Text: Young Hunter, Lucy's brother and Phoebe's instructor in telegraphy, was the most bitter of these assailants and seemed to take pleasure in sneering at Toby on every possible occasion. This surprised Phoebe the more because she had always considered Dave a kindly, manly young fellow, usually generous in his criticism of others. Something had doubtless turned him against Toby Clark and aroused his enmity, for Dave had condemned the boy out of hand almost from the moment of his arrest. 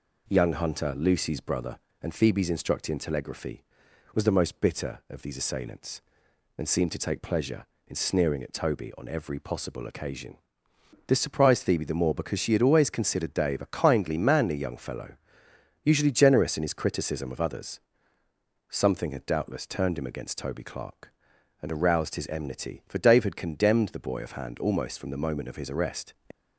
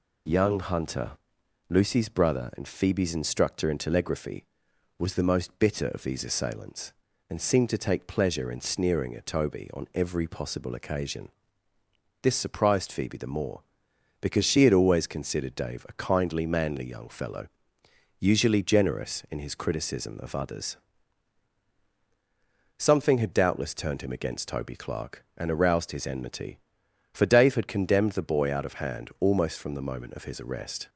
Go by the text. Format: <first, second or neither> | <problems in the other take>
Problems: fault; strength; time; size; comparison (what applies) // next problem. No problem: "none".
second | skips "out"; at 24.2 s